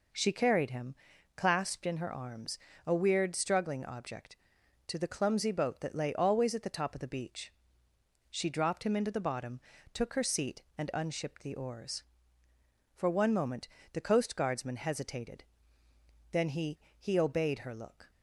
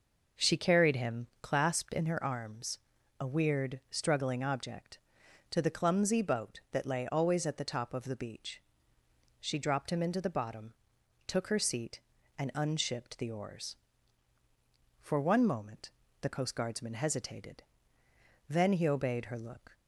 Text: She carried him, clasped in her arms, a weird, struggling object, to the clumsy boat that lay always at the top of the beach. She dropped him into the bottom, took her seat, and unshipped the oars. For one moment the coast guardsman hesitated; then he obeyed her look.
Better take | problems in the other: second | pauses between "moment" and "the"; slight; at 13.6 s; 0.26 s long; slight in the second // says "he" twice; at 16.9 s

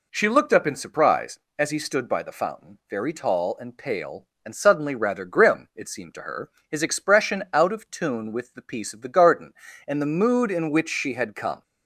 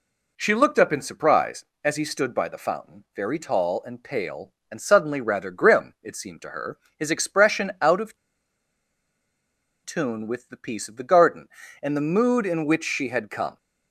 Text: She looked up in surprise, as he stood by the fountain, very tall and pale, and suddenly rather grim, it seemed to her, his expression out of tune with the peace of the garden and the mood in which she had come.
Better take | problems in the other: first | pauses between "of" and "tune"; strong; at 8.1 s; 1.6 s long

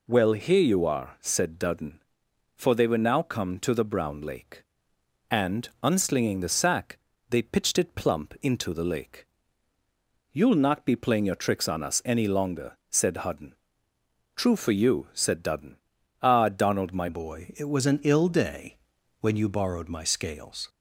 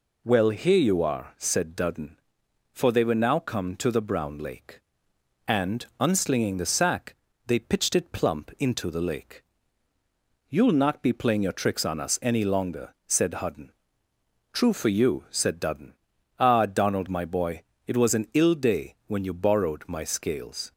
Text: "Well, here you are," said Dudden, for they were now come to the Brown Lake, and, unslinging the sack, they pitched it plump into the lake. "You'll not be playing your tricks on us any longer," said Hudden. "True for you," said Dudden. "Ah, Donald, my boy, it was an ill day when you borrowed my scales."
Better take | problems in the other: second | changes voice at "boy"; from 17.0 s on; 3.6 s long // pauses between "day" and "when"; at 18.7 s; 0.44 s long

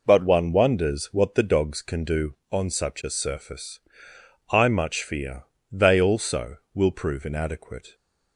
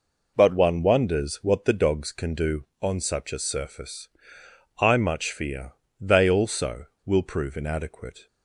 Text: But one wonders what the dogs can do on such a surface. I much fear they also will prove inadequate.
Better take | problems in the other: neither | pauses between "fear" and "they"; slight; the same in both

